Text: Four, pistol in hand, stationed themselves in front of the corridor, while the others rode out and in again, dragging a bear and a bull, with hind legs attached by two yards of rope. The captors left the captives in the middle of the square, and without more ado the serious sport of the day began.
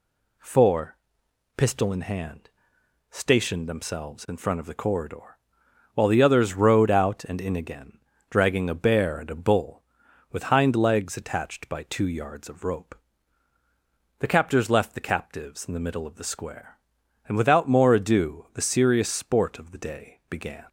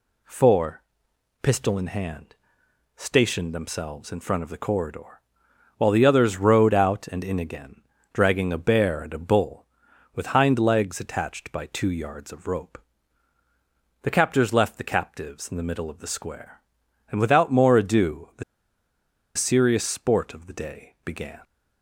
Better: first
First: none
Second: pauses between "the" and "serious"; noticeable; at 18.4 s; 0.92 s long

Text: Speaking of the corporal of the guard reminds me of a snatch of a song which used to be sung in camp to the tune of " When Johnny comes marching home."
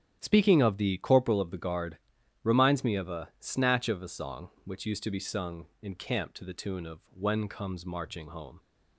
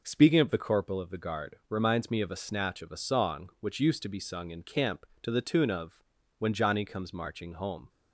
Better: second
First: starts louder than the rest; strong; until 1.2 s; 10.5 dB // pauses between "guard" and "reminds"; noticeable; at 1.9 s; 0.46 s long // skips "Johnny"; at 7.4 s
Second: none

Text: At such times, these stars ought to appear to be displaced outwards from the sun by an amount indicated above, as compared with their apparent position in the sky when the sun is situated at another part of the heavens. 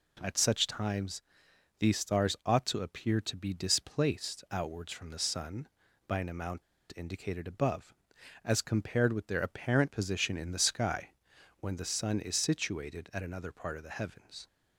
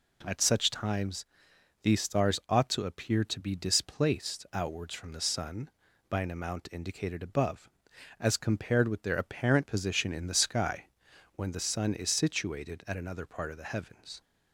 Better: second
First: pauses between "amount" and "indicated"; slight; at 6.6 s; 0.33 s long // pauses between "sky" and "when"; noticeable; at 11.1 s; 0.48 s long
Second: pauses between "sky" and "when"; noticeable; at 10.8 s; 0.48 s long

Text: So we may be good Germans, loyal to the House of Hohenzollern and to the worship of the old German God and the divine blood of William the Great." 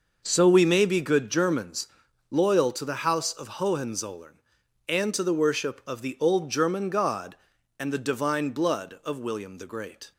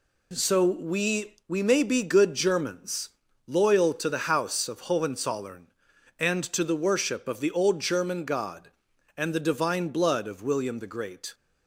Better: first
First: none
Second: says "we" twice; at 1.4 s

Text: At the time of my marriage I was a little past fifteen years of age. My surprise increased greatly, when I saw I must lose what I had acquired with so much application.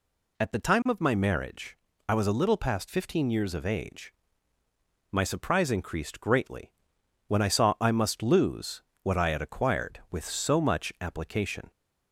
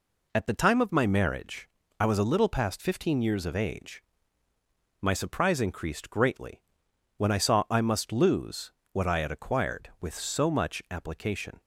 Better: first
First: pauses between "marriage" and "I"; slight; at 1.7 s; 0.32 s long // pauses between "lose" and "what"; slight; at 8.8 s; 0.22 s long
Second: gets quieter; slight; throughout; 3 dB // pauses between "marriage" and "I"; slight; at 1.6 s; 0.32 s long // pauses between "lose" and "what"; slight; at 8.6 s; 0.22 s long

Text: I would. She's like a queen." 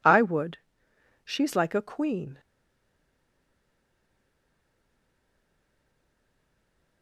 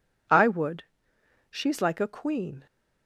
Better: second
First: stays silent after the last word; strong; from 2.3 s on; 4.7 s long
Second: none

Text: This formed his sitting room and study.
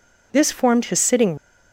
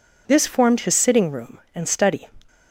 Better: second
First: stops before "room and study"; at 1.3 s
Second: none

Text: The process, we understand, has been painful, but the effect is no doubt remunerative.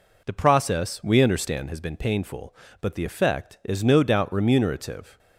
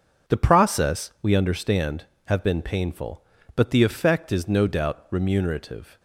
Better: first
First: none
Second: starts louder than the rest; until 1.3 s; 6.5 dB // says "have" for "has"; at 2.2 s

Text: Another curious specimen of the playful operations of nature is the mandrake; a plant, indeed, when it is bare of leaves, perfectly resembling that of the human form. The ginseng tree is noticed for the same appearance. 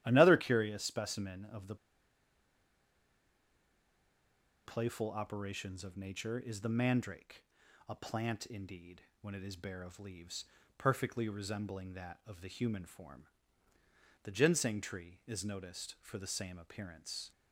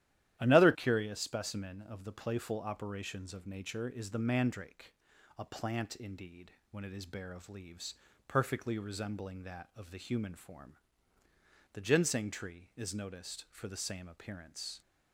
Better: second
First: starts louder than the rest; strong; until 1.0 s; 12.5 dB // pauses between "the" and "playful"; strong; at 1.7 s; 2.8 s long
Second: starts louder than the rest; strong; until 1.4 s; 12.5 dB

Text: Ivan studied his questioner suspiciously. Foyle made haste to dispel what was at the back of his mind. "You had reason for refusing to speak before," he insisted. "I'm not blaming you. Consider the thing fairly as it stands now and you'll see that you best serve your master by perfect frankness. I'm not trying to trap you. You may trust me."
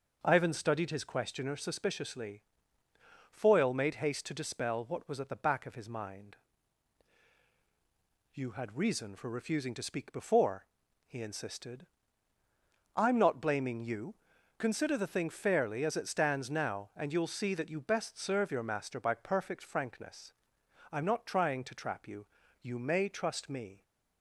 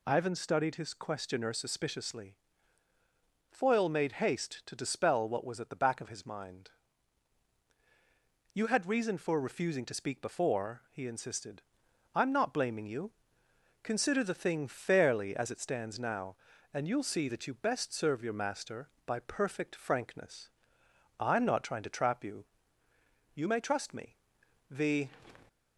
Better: first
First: none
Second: goes on to say "The"; slight; from 24.7 s on; 0.38 s long

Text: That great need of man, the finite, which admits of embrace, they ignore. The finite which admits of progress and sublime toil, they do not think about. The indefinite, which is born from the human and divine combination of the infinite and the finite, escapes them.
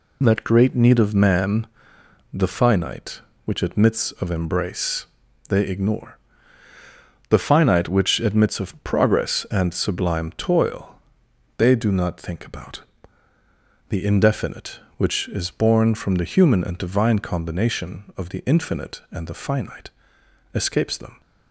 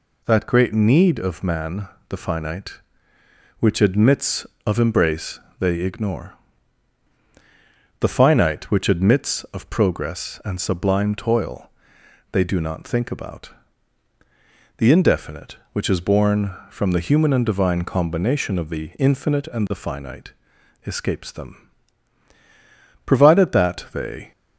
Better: first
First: none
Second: goes on to say "Provided that they"; noticeable; from 23.0 s on; 1.2 s long

